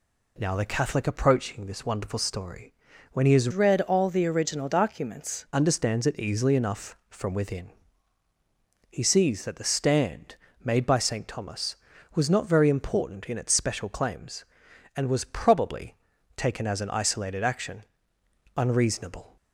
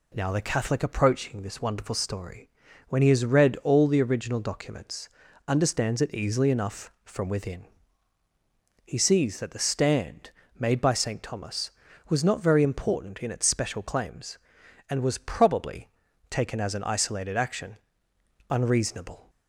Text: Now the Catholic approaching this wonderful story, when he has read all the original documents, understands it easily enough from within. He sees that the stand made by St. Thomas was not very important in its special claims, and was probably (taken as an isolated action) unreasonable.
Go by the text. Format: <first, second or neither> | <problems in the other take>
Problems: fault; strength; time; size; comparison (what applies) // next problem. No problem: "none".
second | changes voice from "read" to "documents"; from 3.5 to 5.4 s; 1.9 s long // pauses between "stand" and "made"; slight; at 10.3 s; 0.30 s long; slight in the second